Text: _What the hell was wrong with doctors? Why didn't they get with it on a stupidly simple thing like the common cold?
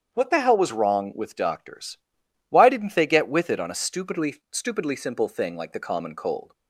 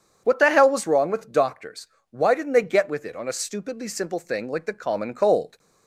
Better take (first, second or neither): second